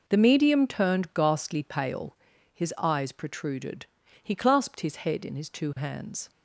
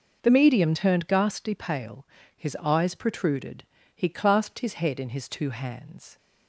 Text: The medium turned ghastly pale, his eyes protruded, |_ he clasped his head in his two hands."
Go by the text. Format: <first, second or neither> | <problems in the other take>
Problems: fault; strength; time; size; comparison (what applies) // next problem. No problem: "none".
neither | none